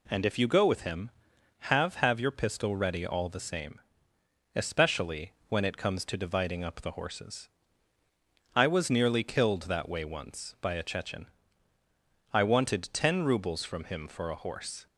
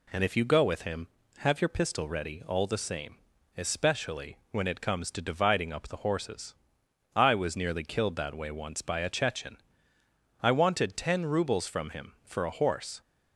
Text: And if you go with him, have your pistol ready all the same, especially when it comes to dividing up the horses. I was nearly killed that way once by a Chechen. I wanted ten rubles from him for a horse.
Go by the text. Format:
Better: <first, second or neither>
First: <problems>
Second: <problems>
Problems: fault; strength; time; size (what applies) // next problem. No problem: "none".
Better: second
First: says "have" twice; at 1.9 s // pauses between "especially" and "when"; slight; at 5.3 s; 0.16 s long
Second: none